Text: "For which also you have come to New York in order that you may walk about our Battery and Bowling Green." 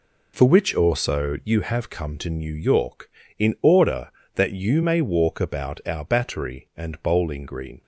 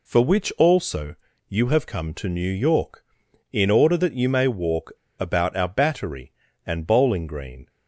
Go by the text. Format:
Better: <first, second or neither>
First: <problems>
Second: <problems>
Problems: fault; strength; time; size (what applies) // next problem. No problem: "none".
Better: first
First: none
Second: pauses between "also" and "you"; slight; at 1.1 s; 0.32 s long // pauses between "walk" and "about"; slight; at 4.9 s; 0.28 s long